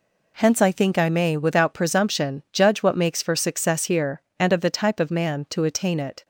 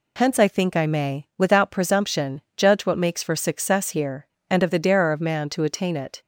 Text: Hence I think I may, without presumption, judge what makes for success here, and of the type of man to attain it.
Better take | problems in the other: first | says "darer" for "type"; at 4.7 s

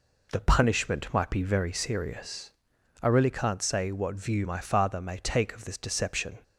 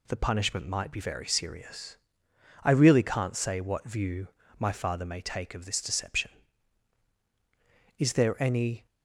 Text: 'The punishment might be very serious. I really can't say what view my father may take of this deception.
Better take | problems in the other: first | pauses between "view" and "my"; slight; at 4.2 s; 0.30 s long // goes on to say "Is there any"; noticeable; from 7.9 s on; 0.88 s long

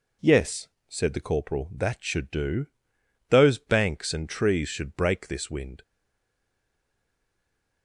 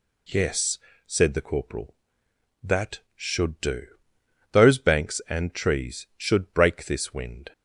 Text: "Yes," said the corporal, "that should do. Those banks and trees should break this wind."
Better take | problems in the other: second | stays silent after the last word; noticeable; from 5.8 s on; 2.0 s long

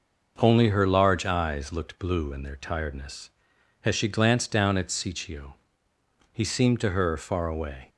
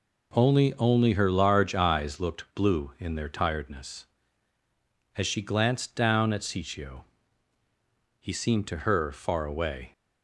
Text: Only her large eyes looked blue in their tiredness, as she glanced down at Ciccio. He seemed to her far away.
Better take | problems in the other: first | says "Only" twice; at 0.7 s

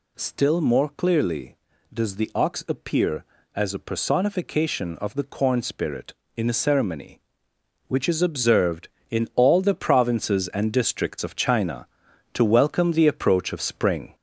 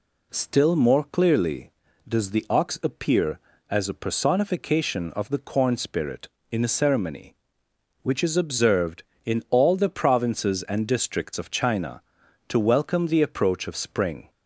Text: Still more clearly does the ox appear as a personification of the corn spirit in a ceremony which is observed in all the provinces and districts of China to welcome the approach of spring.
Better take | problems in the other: second | gets louder; noticeable; throughout; 4.5 dB

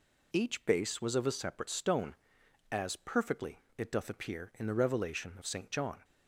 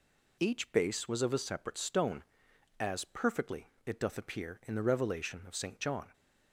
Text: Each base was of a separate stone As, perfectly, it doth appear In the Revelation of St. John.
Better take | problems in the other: neither | none

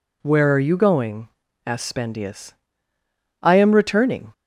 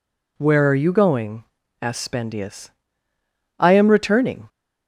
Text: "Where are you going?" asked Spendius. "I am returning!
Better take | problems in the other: neither | none

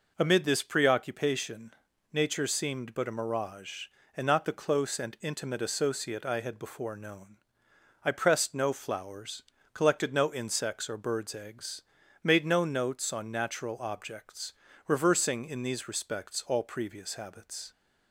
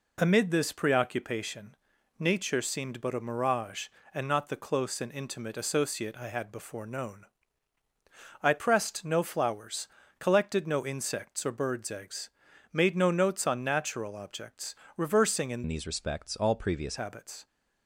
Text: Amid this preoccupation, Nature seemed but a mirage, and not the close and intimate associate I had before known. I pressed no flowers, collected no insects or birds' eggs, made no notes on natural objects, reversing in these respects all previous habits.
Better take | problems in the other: first | changes voice from "these" to "previous"; from 15.6 to 16.9 s; 1.3 s long

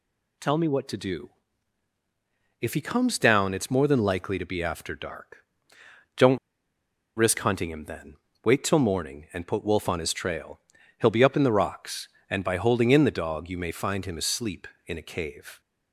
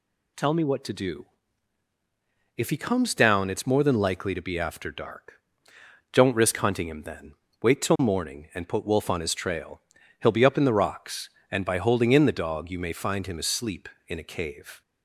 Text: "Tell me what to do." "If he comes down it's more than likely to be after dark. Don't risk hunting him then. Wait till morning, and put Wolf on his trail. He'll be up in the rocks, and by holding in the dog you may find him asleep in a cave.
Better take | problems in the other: second | pauses between "Don't" and "risk"; noticeable; at 6.3 s; 0.78 s long

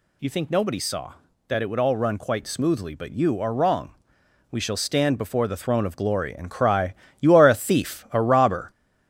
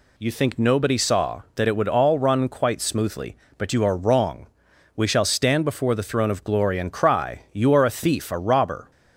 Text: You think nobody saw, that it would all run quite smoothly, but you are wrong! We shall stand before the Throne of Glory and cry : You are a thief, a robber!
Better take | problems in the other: second | gets louder; noticeable; throughout; 5 dB

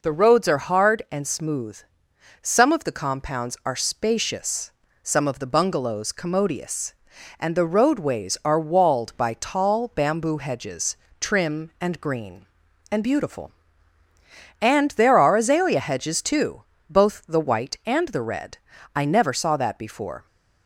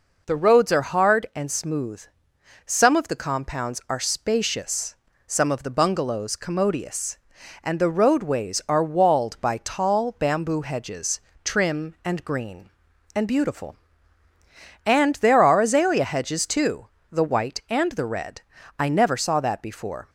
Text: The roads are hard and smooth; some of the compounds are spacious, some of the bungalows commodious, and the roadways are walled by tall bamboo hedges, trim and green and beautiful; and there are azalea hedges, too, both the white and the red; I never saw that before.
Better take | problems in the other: first | skips "both"; at 16.9 s

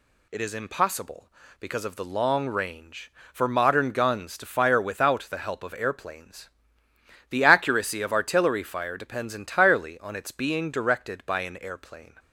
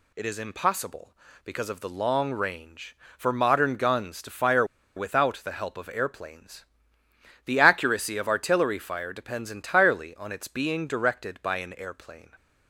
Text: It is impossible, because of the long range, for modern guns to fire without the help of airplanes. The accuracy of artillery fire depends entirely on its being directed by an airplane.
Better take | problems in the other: first | pauses between "fire" and "without"; slight; at 4.6 s; 0.31 s long

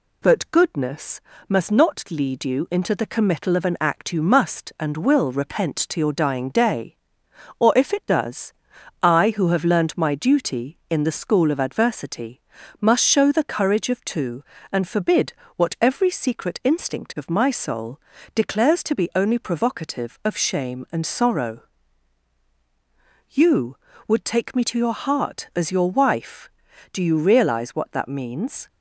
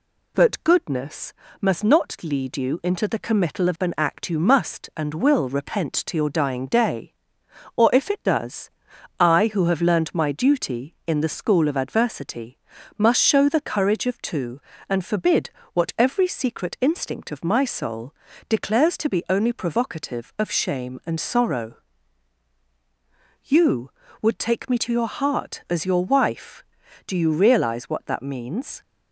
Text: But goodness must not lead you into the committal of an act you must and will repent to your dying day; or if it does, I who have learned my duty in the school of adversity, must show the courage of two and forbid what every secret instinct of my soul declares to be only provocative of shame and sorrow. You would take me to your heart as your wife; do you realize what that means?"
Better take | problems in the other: neither | pauses between "goodness" and "must"; slight; the same in both // pauses between "forbid" and "what"; slight; the same in both // pauses between "soul" and "declares"; slight; the same in both

